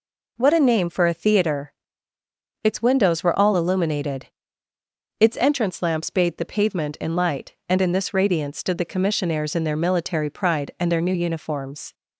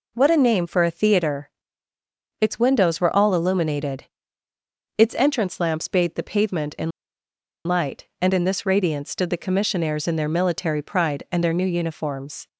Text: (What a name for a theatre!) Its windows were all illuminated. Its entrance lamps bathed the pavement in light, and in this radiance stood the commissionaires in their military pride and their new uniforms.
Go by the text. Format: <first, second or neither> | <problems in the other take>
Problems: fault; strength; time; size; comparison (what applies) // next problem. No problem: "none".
first | pauses between "in" and "light"; noticeable; at 6.9 s; 0.76 s long